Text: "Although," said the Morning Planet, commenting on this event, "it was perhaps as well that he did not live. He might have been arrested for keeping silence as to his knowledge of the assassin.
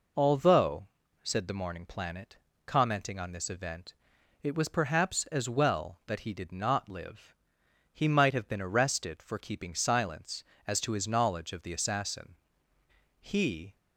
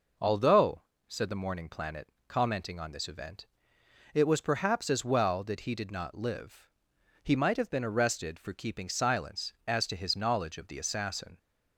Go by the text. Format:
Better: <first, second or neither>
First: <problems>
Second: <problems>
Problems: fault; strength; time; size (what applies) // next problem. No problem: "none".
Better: second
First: goes on to say "He"; from 13.2 s on; 0.56 s long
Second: none